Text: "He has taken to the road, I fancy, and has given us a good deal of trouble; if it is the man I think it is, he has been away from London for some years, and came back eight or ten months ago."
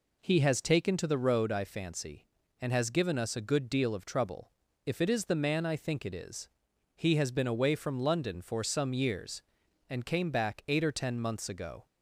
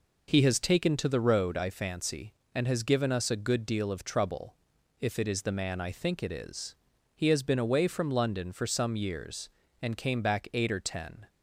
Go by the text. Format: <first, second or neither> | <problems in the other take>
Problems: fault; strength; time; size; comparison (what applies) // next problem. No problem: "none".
first | stops before "months ago"; at 11.2 s